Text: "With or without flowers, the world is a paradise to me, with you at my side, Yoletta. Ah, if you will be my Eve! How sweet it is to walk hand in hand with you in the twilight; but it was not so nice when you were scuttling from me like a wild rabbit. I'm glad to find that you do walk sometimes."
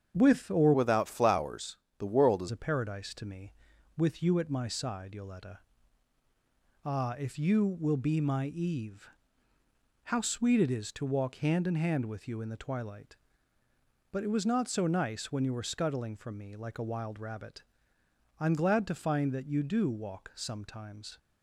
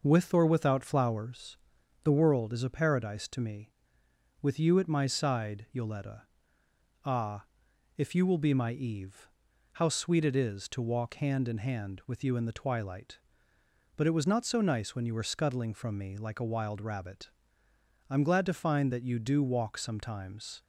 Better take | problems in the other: second | starts louder than the rest; strong; until 1.1 s; 7.5 dB // changes voice from "without" to "is"; from 0.7 to 2.4 s; 1.7 s long

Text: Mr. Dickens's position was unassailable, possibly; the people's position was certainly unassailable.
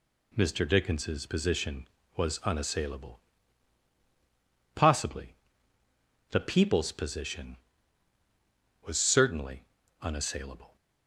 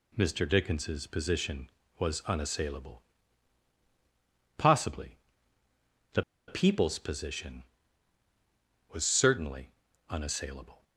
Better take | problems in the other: first | pauses between "the" and "people's"; slight; at 6.2 s; 0.26 s long // pauses between "certainly" and "unassailable"; at 9.7 s; 0.40 s long; also in the first

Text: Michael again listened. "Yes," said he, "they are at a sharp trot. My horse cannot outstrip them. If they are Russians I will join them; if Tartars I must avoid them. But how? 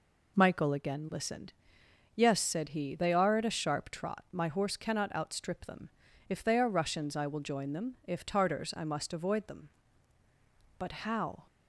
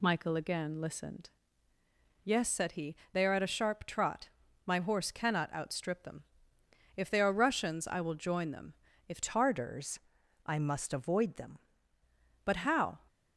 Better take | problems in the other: first | changes voice from "Tartars" to "them"; from 9.2 to 11.5 s; 2.3 s long // pauses between "Tartars" and "I"; at 10.0 s; 0.44 s long

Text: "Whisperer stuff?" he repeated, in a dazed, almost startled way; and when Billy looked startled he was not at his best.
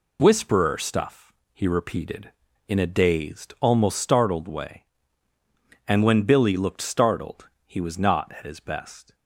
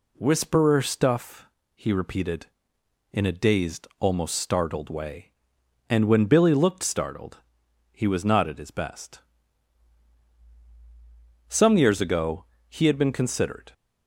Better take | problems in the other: first | pauses between "startled" and "he"; noticeable; at 7.3 s; 0.52 s long; slight in the first // goes on to say "Some years ago he had been considered"; strong; from 11.4 s on; 2.2 s long

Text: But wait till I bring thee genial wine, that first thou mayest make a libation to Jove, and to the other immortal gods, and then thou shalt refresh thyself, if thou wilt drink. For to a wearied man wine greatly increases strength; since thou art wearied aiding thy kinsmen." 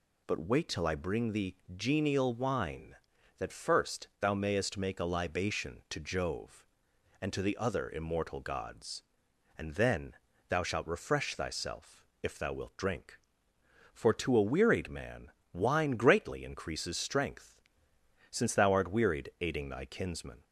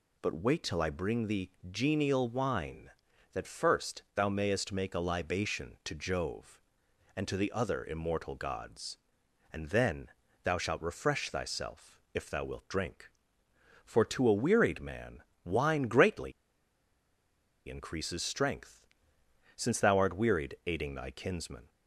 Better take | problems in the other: first | pauses between "thee" and "genial"; slight; at 1.5 s; 0.20 s long; slight in the first // pauses between "then" and "thou"; slight; at 10.0 s; 0.34 s long; slight in the first // pauses between "man" and "wine"; slight; at 15.2 s; 0.22 s long; slight in the first // pauses between "greatly" and "increases"; strong; at 16.3 s; 1.3 s long

